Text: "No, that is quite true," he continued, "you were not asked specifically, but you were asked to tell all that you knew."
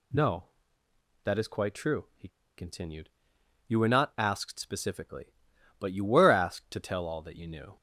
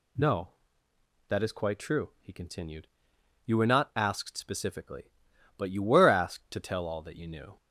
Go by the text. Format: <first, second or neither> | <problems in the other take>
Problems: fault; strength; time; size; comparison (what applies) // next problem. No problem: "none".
second | pauses between "he" and "continued"; slight; at 2.2 s; 0.28 s long